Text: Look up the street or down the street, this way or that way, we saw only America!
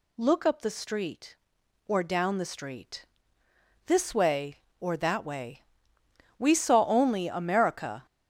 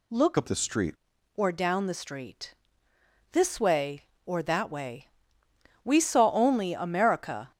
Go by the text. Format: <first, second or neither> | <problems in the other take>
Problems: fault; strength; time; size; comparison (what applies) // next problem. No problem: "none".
first | changes voice from "up" to "street"; from 0.3 to 0.9 s; 0.6 s long